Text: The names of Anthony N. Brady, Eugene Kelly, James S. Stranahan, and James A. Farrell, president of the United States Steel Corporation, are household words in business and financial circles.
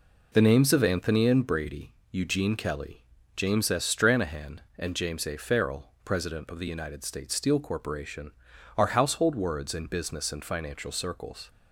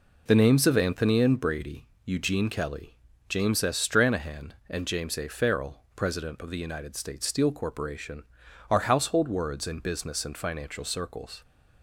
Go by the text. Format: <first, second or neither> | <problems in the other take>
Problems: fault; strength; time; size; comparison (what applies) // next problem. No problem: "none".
neither | none